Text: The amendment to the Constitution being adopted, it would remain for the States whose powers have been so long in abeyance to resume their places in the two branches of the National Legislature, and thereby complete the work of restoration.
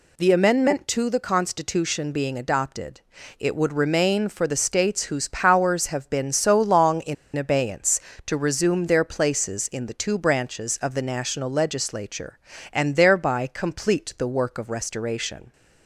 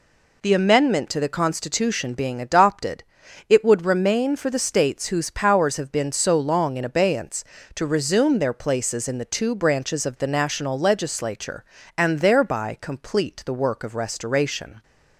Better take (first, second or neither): second